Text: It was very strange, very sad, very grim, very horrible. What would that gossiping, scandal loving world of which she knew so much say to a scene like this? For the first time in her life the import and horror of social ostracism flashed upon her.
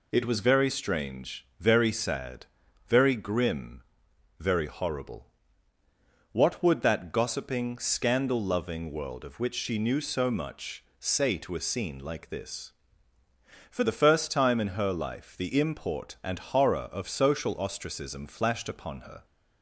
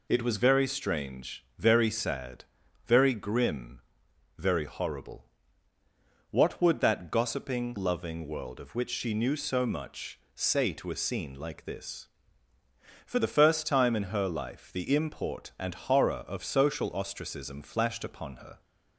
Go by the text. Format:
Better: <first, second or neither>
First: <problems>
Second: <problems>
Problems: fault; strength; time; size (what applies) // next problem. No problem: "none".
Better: first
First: pauses between "much" and "say"; slight; at 10.8 s; 0.16 s long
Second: skips "scandal"; at 7.7 s // pauses between "much" and "say"; slight; at 10.1 s; 0.16 s long